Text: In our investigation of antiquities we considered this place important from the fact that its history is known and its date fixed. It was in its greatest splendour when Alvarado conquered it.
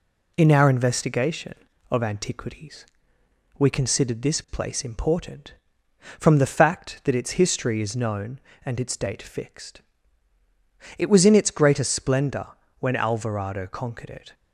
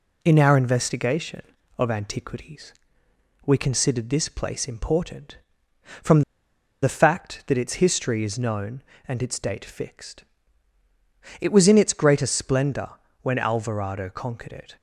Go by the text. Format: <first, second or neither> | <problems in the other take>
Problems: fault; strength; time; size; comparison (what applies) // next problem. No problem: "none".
first | pauses between "antiquities" and "we"; noticeable; at 2.7 s; 0.72 s long; noticeable in the first // pauses between "from" and "the"; noticeable; at 6.2 s; 0.61 s long // pauses between "splendour" and "when"; slight; at 12.9 s; 0.28 s long; slight in the first